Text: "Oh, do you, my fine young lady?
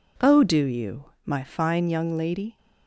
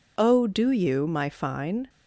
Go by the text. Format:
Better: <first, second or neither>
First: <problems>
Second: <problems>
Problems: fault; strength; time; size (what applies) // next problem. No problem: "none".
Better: first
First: none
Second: stops before "young lady"; at 1.8 s